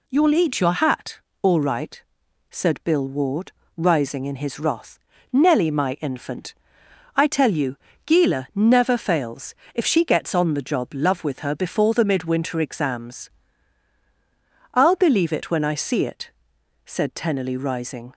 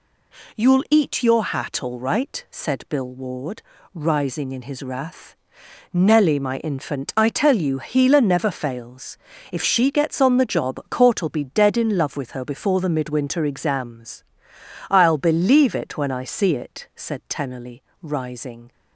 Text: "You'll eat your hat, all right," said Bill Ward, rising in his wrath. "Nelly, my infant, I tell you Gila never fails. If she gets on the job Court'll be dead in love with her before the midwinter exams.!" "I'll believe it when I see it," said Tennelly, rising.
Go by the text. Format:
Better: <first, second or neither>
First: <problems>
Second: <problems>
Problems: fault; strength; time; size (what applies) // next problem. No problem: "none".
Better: second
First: pauses between "you" and "Gila"; slight; at 7.7 s; 0.28 s long // skips "Court'll be dead in"; at 10.9 s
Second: none